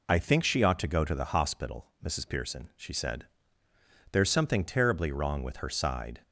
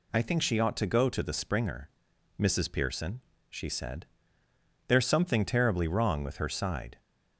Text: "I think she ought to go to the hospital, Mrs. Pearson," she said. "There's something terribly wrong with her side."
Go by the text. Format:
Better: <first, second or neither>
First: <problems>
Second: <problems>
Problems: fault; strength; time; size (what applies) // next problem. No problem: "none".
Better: first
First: none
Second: says "springer" for "hospital"; at 1.3 s